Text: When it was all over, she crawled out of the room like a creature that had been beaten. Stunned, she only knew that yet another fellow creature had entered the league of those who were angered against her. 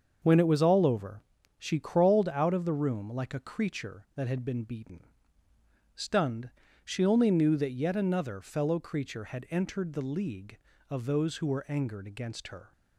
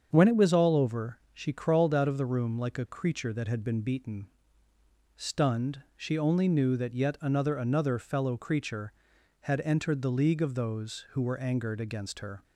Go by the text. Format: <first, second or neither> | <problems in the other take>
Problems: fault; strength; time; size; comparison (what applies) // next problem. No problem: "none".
first | starts louder than the rest; strong; until 1.1 s; 7 dB; also in the first // says "another" twice; at 7.5 s